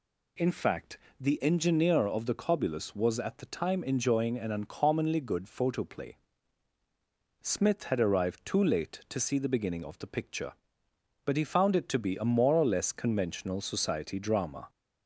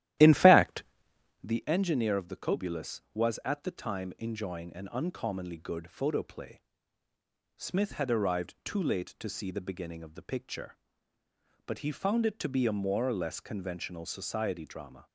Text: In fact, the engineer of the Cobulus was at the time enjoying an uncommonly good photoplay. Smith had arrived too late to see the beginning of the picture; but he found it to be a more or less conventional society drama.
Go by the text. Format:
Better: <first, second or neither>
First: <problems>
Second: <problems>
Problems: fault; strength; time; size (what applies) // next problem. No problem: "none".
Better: first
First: none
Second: starts louder than the rest; strong; until 1.6 s; 13.5 dB